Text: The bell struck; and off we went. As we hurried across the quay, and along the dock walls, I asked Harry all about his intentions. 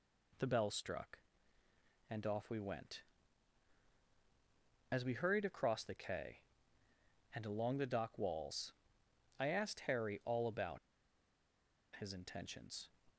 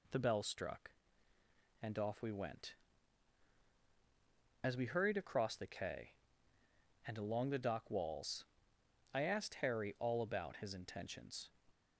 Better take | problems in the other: second | pauses between "about" and "his"; at 10.7 s; 1.1 s long

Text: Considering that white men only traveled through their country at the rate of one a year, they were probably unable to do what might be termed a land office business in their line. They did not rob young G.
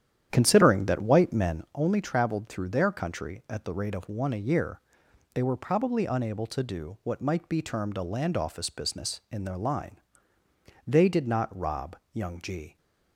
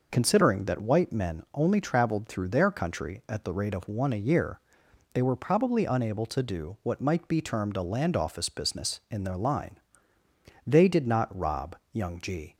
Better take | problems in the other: second | starts louder than the rest; strong; until 1.8 s; 10 dB // pauses between "rob" and "young"; slight; at 11.9 s; 0.16 s long; slight in the second

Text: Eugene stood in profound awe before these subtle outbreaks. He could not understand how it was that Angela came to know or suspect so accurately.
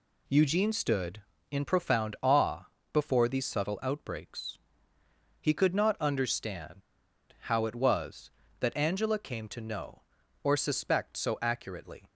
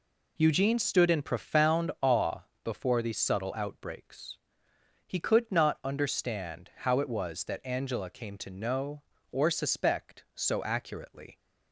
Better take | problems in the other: second | pauses between "awe" and "before"; slight; at 2.6 s; 0.26 s long; slight in the second // pauses between "understand" and "how"; noticeable; at 6.8 s; 0.60 s long

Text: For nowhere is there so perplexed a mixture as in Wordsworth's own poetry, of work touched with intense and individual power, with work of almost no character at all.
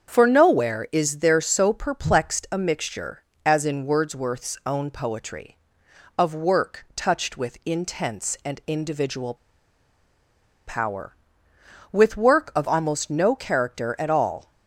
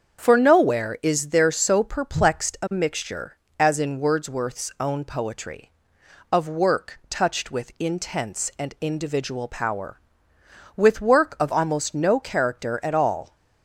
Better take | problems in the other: second | starts louder than the rest; until 1.1 s; 7 dB; also in the second // pauses between "individual" and "power"; strong; at 9.3 s; 1.3 s long

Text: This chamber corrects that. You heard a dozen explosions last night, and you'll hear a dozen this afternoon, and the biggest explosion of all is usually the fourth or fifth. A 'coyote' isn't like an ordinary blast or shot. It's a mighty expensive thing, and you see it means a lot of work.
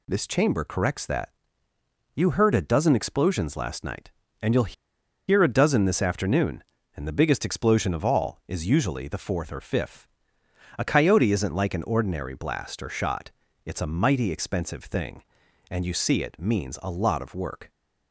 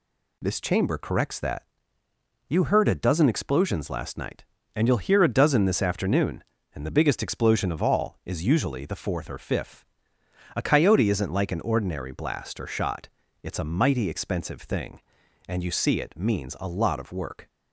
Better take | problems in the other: second | pauses between "you'll" and "hear"; noticeable; at 4.7 s; 0.55 s long

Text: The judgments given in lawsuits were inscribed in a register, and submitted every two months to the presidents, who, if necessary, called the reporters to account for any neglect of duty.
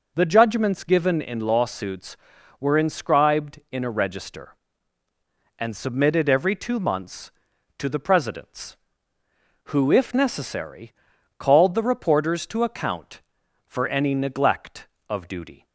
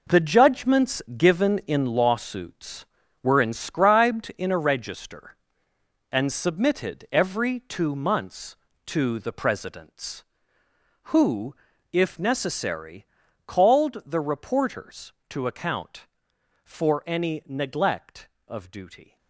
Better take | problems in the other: first | gets quieter; strong; throughout; 11.5 dB // pauses between "judgments" and "given"; slight; at 1.0 s; 0.16 s long

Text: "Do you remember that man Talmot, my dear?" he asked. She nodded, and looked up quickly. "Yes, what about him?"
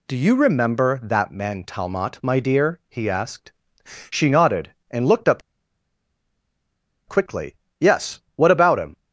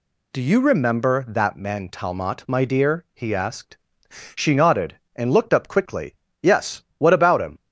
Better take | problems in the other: second | pauses between "up" and "quickly"; strong; at 5.4 s; 1.6 s long

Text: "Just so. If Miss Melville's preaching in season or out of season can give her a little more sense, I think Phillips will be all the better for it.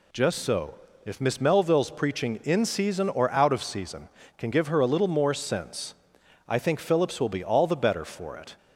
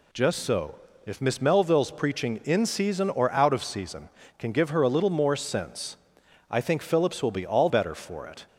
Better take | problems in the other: first | skips "the"; at 7.6 s

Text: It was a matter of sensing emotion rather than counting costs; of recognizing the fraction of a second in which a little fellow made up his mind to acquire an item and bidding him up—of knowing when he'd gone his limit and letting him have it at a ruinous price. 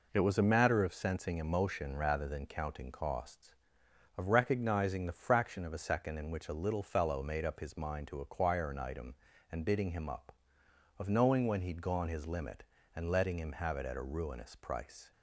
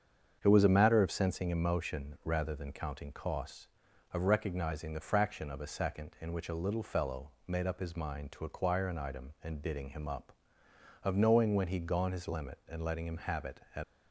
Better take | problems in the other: first | starts louder than the rest; strong; until 1.4 s; 7.5 dB // stops before "a ruinous price"; at 13.8 s

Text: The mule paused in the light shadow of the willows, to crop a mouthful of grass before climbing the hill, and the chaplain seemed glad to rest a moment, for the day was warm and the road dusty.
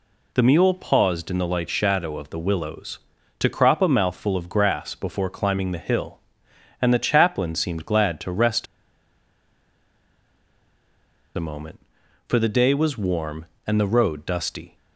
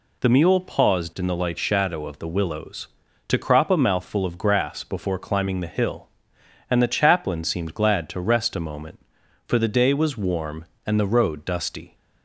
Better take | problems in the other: second | pauses between "rest" and "a"; strong; at 8.6 s; 2.7 s long

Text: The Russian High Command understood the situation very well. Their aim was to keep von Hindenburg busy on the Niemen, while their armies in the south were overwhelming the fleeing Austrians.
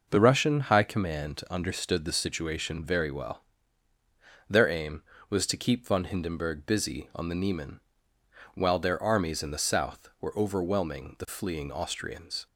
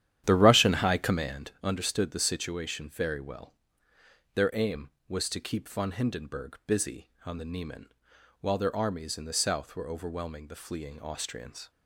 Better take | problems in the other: first | starts louder than the rest; strong; until 1.3 s; 11 dB

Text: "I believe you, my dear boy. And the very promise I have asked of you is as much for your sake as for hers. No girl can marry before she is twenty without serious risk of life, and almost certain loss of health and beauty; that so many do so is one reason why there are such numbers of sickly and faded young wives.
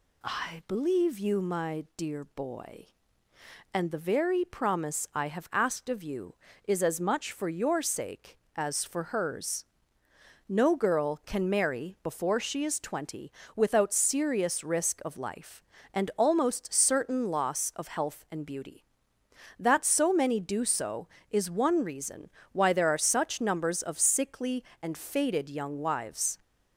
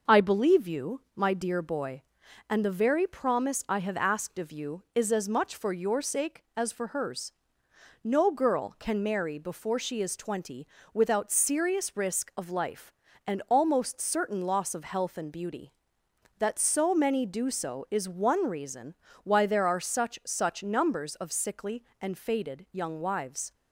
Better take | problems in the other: first | pauses between "twenty" and "without"; slight; at 10.6 s; 0.26 s long; slight in the first // pauses between "reason" and "why"; slight; at 18.9 s; 0.30 s long; slight in the first // says "such" twice; at 20.2 s

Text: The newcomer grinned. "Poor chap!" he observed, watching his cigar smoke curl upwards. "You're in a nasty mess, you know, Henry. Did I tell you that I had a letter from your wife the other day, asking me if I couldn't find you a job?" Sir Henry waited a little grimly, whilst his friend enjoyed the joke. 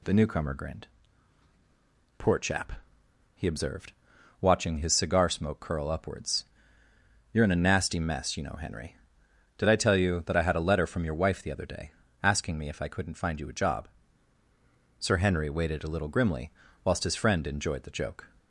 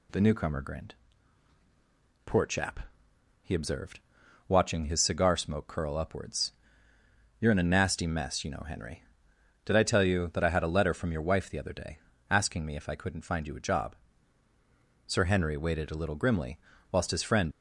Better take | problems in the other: first | stops before "enjoyed the joke"; at 17.5 s

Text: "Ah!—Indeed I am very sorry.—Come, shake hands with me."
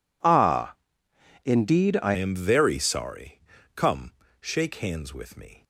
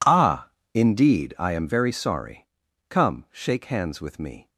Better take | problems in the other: second | changes voice at "am"; from 2.1 s on; 3.5 s long

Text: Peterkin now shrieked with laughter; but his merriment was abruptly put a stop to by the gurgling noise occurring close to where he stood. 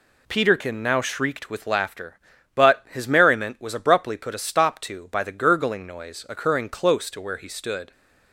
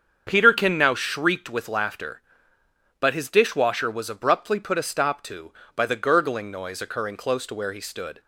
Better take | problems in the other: first | starts louder than the rest; strong; until 1.2 s; 7.5 dB // says "dishwasher" for "merriment"; at 3.2 s

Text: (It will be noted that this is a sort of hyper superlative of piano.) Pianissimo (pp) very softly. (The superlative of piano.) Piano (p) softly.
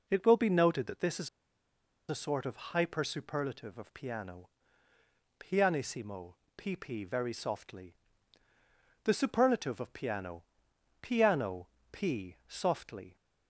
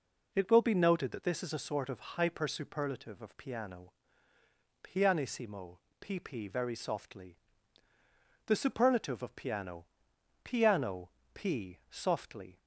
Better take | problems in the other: second | pauses between "is" and "a"; noticeable; at 1.2 s; 0.80 s long // pauses between "Piano" and "p"; slight; at 11.6 s; 0.24 s long; slight in the second

